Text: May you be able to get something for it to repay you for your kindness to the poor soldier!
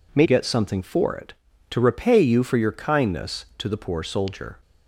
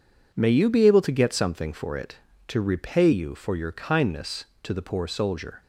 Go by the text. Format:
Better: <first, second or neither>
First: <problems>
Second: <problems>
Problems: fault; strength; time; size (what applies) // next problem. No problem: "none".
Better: second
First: skips "you be able to"; at 0.2 s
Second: none